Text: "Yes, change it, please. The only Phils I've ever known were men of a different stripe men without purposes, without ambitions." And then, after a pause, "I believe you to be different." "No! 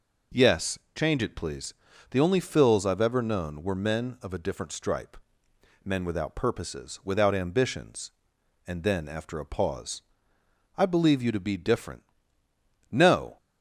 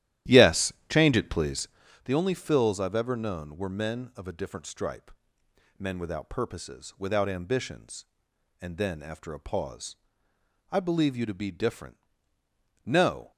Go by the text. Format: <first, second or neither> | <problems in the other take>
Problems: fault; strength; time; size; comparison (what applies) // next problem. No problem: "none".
first | starts louder than the rest; strong; until 2.0 s; 13 dB // pauses between "stripe" and "men"; noticeable; at 5.1 s; 0.68 s long; noticeable in the first